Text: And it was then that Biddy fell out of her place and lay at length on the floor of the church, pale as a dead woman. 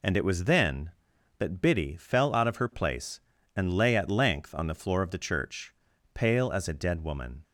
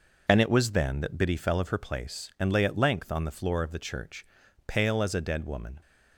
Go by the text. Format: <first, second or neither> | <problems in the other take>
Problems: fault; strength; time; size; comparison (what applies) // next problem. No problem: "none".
first | skips "out"; at 1.5 s